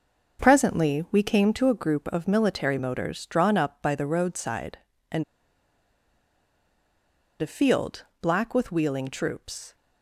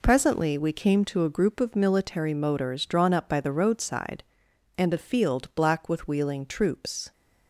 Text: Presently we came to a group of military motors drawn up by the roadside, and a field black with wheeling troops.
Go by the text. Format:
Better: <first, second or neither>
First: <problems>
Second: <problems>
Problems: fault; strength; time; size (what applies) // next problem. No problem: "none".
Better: second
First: starts louder than the rest; noticeable; until 1.4 s; 6 dB // pauses between "and" and "a"; strong; at 5.2 s; 2.1 s long // pauses between "field" and "black"; slight; at 8.0 s; 0.16 s long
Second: none